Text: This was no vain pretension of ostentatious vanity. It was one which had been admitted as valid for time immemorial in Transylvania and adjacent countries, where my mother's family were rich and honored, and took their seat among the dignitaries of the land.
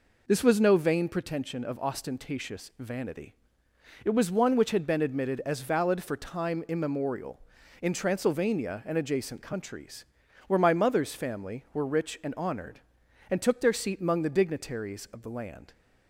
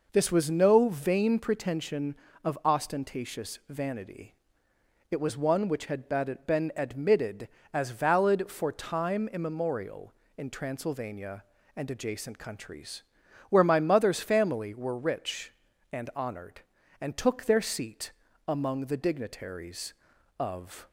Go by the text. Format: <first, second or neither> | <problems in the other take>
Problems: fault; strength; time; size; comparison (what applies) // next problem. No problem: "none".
first | pauses between "seat" and "among"; slight; at 18.1 s; 0.36 s long // stops before "the land"; at 20.8 s